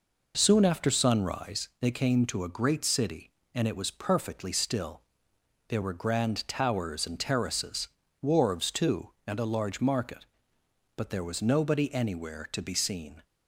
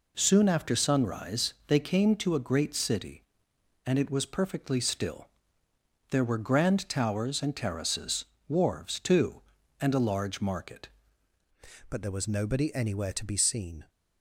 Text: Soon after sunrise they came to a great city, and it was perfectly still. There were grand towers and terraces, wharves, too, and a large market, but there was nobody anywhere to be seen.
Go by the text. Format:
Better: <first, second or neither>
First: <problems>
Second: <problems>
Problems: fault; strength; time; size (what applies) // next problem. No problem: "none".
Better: first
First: none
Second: pauses between "sunrise" and "they"; slight; at 1.5 s; 0.16 s long // changes voice at "but"; from 11.8 s on; 2.0 s long